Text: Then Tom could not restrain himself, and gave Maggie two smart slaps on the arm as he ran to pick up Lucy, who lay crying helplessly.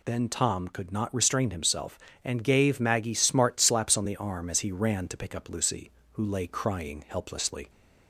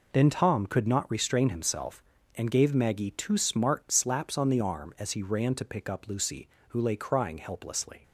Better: second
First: skips "two"; at 3.1 s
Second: none

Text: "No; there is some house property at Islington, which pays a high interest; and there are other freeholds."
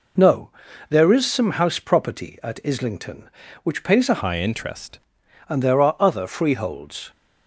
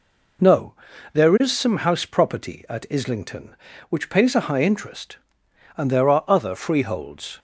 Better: second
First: changes voice from "high" to "interest"; from 4.2 to 5.0 s; 0.8 s long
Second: none

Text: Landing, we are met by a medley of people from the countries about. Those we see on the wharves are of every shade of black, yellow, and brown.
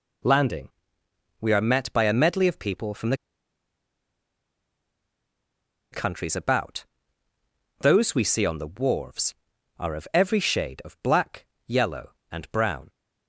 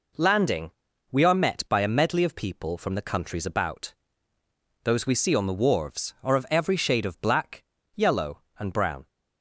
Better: second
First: pauses between "the" and "countries"; strong; at 3.1 s; 2.7 s long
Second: none

